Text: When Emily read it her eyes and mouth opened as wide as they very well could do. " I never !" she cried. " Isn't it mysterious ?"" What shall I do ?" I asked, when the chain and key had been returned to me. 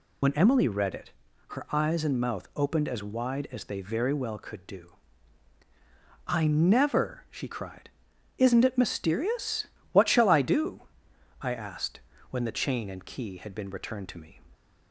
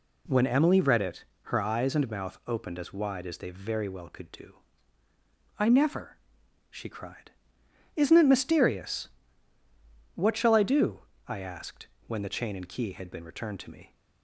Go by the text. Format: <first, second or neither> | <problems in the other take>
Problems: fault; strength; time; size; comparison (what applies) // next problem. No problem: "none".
second | loses the start of "When"; at 0.2 s; 65 ms // pauses between "it" and "her"; at 1.1 s; 0.38 s long; slight in the second